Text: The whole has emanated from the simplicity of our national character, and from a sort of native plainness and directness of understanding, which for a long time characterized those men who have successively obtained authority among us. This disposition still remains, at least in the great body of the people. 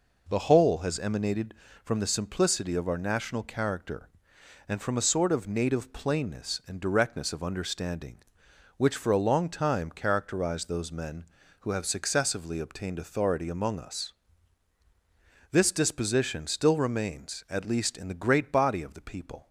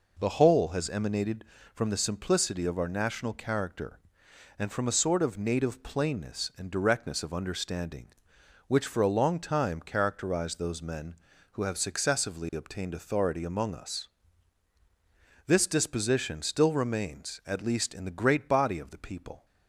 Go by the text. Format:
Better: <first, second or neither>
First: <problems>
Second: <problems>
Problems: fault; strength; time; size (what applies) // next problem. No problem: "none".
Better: neither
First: none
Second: none